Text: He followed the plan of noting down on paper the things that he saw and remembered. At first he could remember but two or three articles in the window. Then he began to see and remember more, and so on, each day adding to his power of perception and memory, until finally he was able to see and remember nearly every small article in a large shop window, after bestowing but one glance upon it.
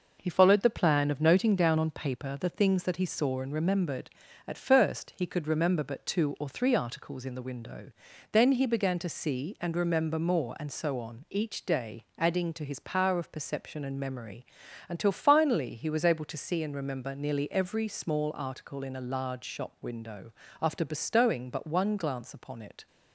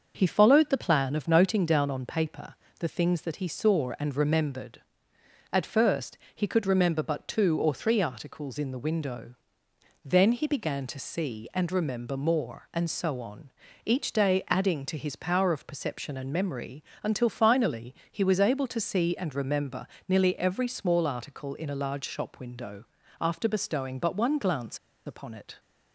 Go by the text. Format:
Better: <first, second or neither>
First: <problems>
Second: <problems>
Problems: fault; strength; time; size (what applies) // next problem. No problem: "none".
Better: first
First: none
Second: starts louder than the rest; until 1.1 s; 6.5 dB // pauses between "paper" and "the"; slight; at 2.5 s; 0.26 s long // pauses between "first" and "he"; slight; at 6.1 s; 0.18 s long // pauses between "finally" and "he"; slight; at 17.9 s; 0.16 s long // pauses between "remember" and "nearly"; slight; at 19.8 s; 0.22 s long // pauses between "glance" and "upon"; slight; at 24.7 s; 0.28 s long